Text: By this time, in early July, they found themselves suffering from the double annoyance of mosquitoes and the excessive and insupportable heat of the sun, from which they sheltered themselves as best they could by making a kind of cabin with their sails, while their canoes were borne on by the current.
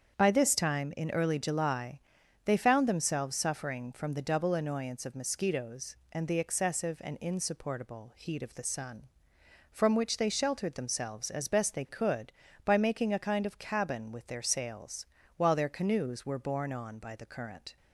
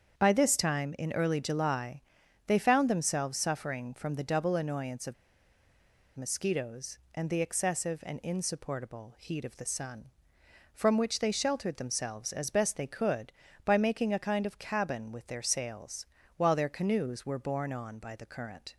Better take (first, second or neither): first